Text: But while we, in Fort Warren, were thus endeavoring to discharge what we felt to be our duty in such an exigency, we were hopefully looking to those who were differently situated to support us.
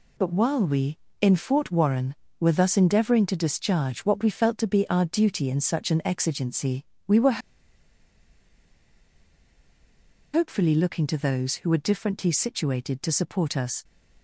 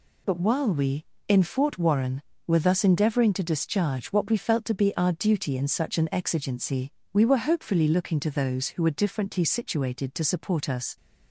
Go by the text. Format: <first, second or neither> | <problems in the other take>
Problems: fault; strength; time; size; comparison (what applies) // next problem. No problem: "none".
second | pauses between "were" and "hopefully"; strong; at 7.4 s; 2.9 s long